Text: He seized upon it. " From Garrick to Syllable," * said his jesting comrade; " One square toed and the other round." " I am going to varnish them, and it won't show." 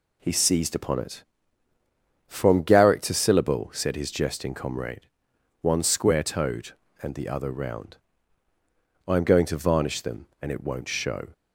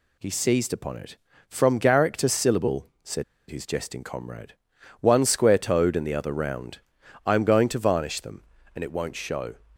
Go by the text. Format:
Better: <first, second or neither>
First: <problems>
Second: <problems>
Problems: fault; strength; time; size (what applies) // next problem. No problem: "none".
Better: first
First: none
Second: pauses between "said" and "his"; slight; at 3.2 s; 0.26 s long